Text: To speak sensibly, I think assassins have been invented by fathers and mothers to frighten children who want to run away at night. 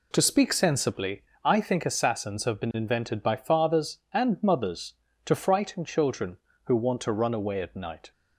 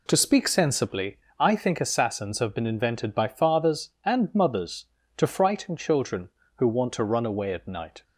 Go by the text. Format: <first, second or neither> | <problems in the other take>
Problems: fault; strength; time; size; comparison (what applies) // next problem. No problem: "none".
neither | none